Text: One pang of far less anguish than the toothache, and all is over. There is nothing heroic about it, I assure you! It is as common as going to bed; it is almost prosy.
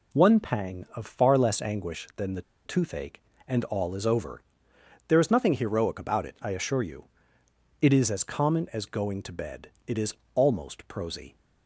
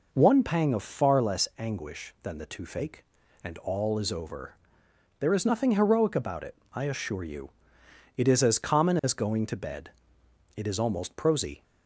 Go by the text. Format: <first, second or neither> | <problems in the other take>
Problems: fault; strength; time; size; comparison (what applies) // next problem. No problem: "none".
second | pauses between "the" and "toothache"; slight; at 2.4 s; 0.24 s long // pauses between "is" and "almost"; slight; at 10.1 s; 0.18 s long